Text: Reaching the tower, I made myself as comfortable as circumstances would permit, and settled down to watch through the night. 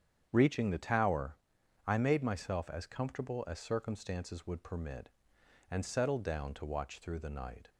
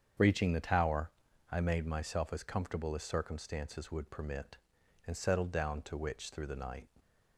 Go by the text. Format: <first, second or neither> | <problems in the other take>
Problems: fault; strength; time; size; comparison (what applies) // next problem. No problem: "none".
first | starts louder than the rest; strong; until 1.5 s; 7.5 dB; strong in the first // says "witch" for "watch"; at 5.9 s